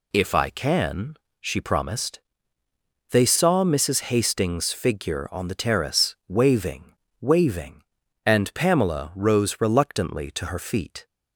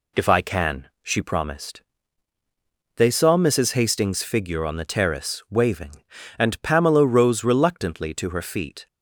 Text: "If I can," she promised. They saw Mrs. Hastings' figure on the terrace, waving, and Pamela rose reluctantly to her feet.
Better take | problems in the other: second | says "waving" twice; at 7.2 s

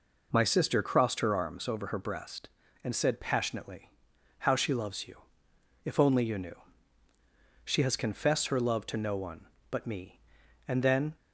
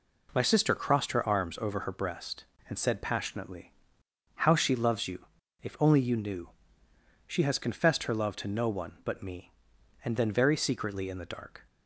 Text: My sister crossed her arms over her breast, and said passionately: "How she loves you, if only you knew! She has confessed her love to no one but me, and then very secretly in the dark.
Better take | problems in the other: second | stops before "very secretly in the dark"; at 11.1 s

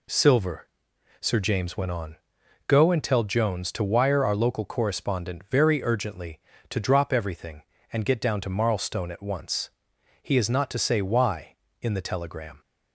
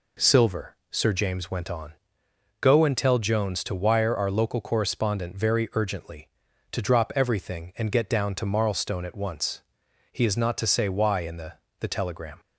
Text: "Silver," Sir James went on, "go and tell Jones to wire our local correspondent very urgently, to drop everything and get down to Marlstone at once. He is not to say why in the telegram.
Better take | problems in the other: first | says "the" twice; at 11.7 s

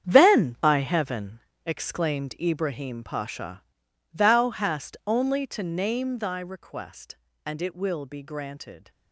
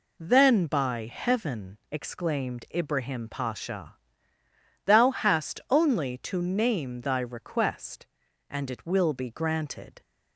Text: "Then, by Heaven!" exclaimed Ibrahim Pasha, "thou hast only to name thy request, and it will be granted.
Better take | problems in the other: second | gets quieter; strong; throughout; 11.5 dB

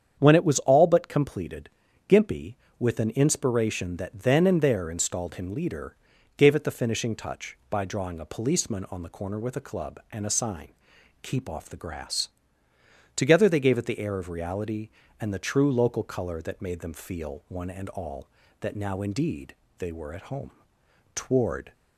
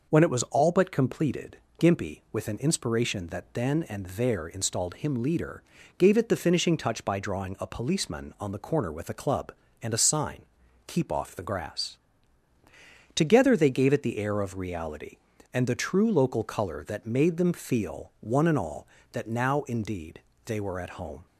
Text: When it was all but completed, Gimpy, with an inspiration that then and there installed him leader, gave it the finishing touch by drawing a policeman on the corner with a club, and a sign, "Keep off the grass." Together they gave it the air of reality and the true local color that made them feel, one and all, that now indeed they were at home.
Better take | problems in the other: second | starts louder than the rest; strong; until 1.2 s; 8.5 dB // pauses between "indeed" and "they"; slight; at 19.5 s; 0.22 s long; slight in the second // goes on to say "Toward"; from 21.1 s on; 0.58 s long

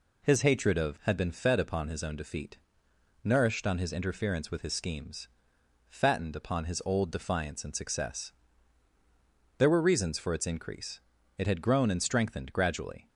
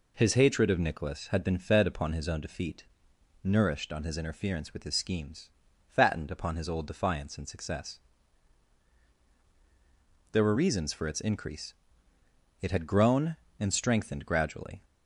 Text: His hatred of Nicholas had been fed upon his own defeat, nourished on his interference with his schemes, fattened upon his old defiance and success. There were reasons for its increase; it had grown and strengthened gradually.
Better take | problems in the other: second | skips "Nicholas"; at 0.9 s

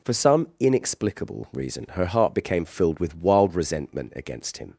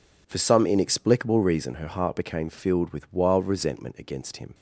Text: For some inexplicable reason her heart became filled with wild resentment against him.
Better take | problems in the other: neither | none

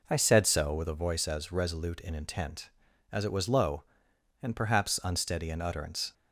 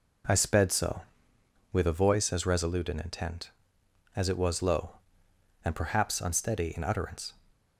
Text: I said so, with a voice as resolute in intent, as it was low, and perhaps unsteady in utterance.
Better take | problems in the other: first | says "sped" for "said"; at 0.3 s

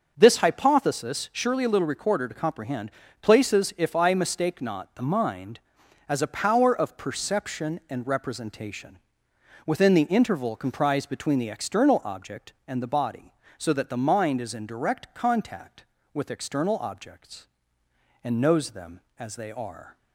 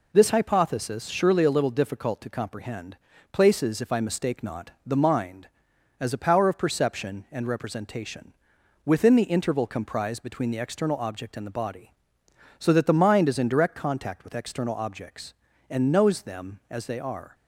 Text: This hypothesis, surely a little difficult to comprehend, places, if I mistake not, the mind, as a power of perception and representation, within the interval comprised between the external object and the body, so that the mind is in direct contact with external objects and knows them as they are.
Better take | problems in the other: second | starts louder than the rest; until 1.1 s; 6.5 dB // says "recorder" for "difficult"; at 1.8 s

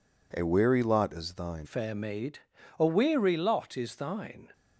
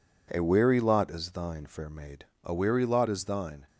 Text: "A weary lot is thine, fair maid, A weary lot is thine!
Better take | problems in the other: second | changes voice at "fair"; from 1.6 s on; 2.9 s long

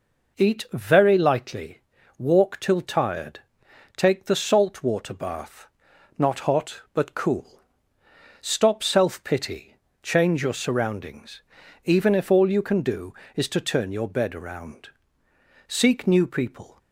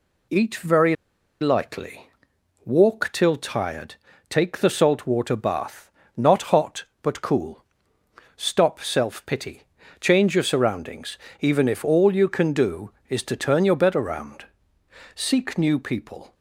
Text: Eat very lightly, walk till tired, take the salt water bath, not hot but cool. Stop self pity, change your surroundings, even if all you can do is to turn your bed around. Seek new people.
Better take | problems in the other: first | pauses between "very" and "lightly"; noticeable; at 0.9 s; 0.46 s long

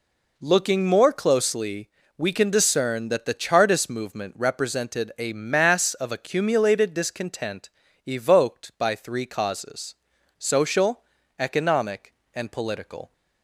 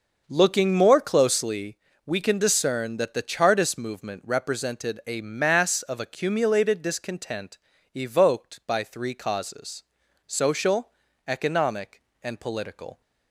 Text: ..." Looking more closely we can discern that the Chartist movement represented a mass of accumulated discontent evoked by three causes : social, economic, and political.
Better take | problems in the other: first | starts louder than the rest; noticeable; until 1.7 s; 6 dB // pauses between "closely" and "we"; slight; at 1.7 s; 0.30 s long; slight in the first // pauses between "discontent" and "evoked"; at 7.5 s; 0.38 s long; also in the first

